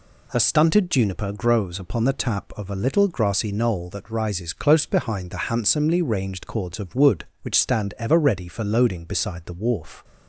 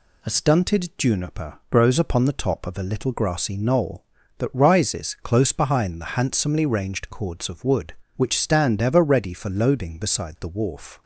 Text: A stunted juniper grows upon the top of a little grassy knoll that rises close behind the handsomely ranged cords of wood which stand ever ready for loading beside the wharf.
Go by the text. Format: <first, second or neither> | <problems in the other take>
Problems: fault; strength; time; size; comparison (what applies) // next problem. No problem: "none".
second | says "tap" for "top"; at 2.1 s